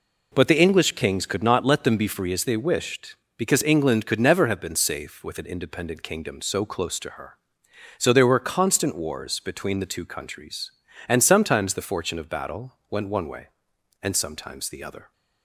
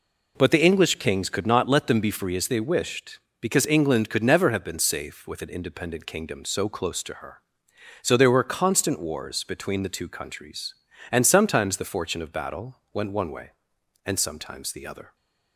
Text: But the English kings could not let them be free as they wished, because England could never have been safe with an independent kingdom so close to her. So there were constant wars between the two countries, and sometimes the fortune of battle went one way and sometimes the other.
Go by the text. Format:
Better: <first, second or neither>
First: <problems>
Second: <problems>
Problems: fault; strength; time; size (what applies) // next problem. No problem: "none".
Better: neither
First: pauses between "battle" and "went"; slight; at 12.7 s; 0.18 s long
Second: pauses between "battle" and "went"; slight; at 12.7 s; 0.18 s long